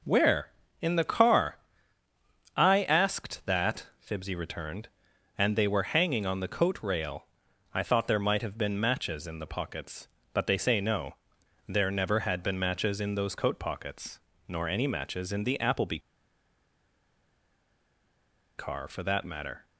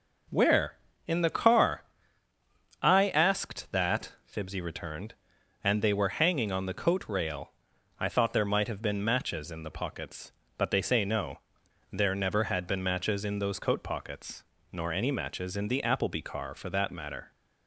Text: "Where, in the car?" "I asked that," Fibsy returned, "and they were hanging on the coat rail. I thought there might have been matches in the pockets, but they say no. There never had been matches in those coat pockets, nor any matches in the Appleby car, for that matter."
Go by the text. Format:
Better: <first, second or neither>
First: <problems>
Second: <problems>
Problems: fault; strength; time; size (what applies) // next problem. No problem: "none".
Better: second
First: pauses between "Appleby" and "car"; strong; at 15.9 s; 2.5 s long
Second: none